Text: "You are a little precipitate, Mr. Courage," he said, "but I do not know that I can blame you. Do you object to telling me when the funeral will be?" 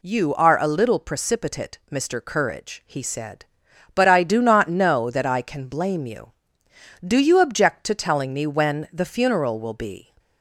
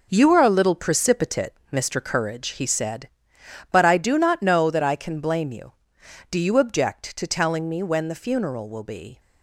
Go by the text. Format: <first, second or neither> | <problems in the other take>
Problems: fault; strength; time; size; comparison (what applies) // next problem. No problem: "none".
first | gets quieter; strong; throughout; 9.5 dB